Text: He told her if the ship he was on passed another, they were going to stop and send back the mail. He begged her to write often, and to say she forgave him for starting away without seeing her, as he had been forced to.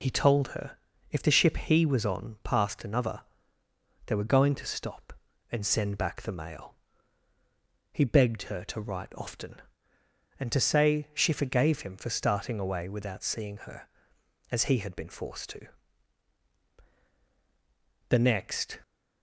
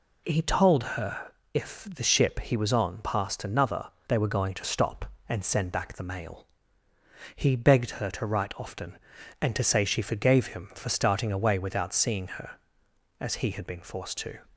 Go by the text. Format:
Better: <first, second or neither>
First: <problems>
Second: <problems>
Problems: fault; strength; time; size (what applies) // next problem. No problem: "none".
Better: second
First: pauses between "her" and "if"; slight; at 0.7 s; 0.34 s long // goes on to say "The next"; noticeable; from 18.0 s on; 0.72 s long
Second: pauses between "her" and "if"; slight; at 1.2 s; 0.24 s long